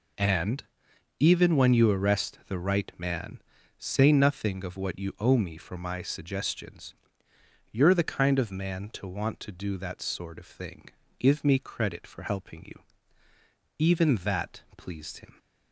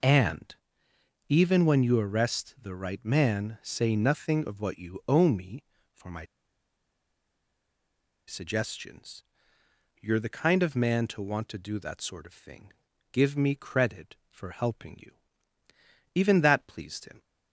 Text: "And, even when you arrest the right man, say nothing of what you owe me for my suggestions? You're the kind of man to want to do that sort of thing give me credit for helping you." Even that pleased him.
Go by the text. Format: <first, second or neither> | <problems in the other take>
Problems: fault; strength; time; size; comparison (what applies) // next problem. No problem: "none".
first | pauses between "my" and "suggestions"; strong; at 6.2 s; 2.0 s long // pauses between "thing" and "give"; at 12.7 s; 0.40 s long; slight in the first